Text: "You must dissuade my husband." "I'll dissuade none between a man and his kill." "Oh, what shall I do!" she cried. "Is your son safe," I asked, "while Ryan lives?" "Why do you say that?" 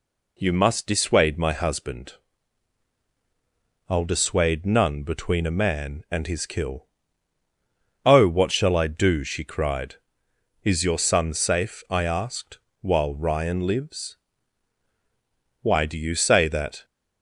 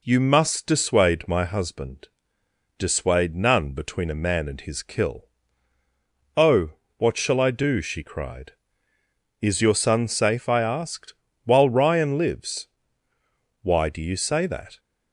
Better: first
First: none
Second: skips "I'll"; at 2.4 s

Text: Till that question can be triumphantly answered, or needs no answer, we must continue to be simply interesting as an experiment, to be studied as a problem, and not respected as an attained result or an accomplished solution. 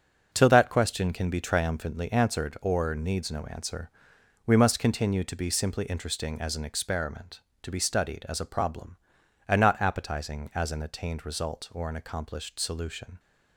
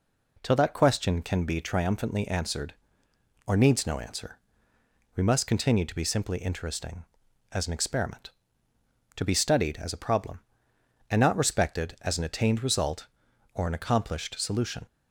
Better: second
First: starts louder than the rest; until 1.3 s; 7 dB // says "appetizing" for "respected"; at 9.7 s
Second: none

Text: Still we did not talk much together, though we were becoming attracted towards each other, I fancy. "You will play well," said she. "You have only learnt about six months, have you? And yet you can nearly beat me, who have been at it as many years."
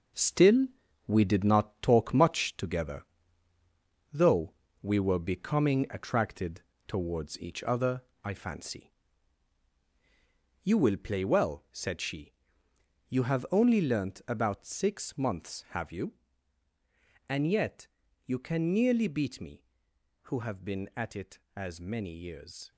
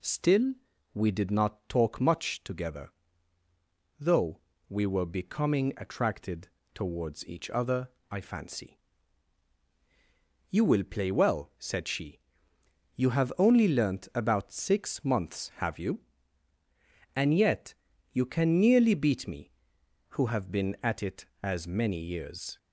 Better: second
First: gets quieter; strong; throughout; 7.5 dB // pauses between "Still" and "we"; at 0.6 s; 0.40 s long // pauses between "though" and "we"; slight; at 4.5 s; 0.28 s long // pauses between "attracted" and "towards"; slight; at 6.6 s; 0.26 s long // pauses between "yet" and "you"; slight; at 17.8 s; 0.36 s long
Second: pauses between "Still" and "we"; at 0.5 s; 0.40 s long // pauses between "though" and "we"; slight; at 4.3 s; 0.28 s long // pauses between "attracted" and "towards"; slight; at 6.4 s; 0.26 s long // pauses between "yet" and "you"; slight; at 17.7 s; 0.36 s long

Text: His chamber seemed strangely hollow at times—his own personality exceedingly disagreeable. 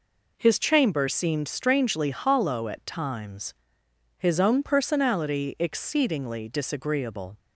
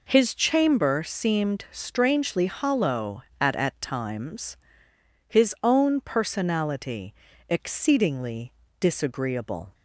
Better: first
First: none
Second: says "at" twice; at 3.5 s // pauses between "personality" and "exceedingly"; at 7.1 s; 0.38 s long // pauses between "exceedingly" and "disagreeable"; slight; at 8.5 s; 0.26 s long

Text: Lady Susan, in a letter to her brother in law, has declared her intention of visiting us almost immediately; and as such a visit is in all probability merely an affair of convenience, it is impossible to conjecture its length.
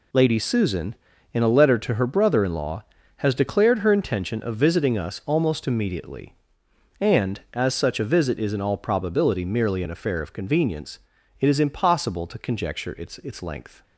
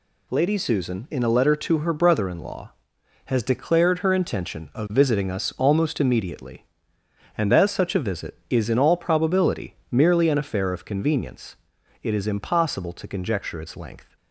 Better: second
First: says "its" twice; at 13.1 s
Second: none

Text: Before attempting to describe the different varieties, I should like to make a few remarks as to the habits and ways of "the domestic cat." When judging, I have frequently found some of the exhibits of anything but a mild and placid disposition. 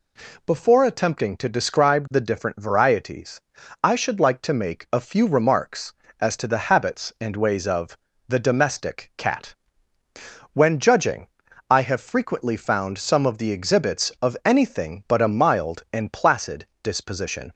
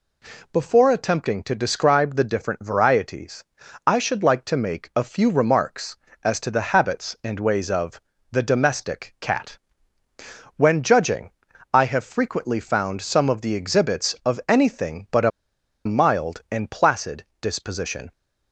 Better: first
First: pauses between "of" and "the"; slight; at 7.9 s; 0.32 s long // pauses between "placid" and "disposition"; slight; at 16.6 s; 0.16 s long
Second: pauses between "of" and "the"; slight; at 7.9 s; 0.32 s long // pauses between "a" and "mild"; noticeable; at 15.3 s; 0.55 s long // pauses between "placid" and "disposition"; slight; at 17.2 s; 0.16 s long

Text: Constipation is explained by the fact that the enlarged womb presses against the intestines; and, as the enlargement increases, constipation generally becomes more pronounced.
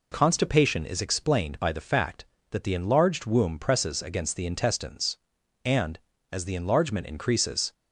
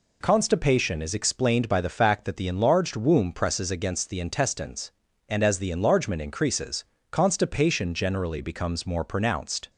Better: second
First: stops before "constipation generally becomes more pronounced"; at 7.7 s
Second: none

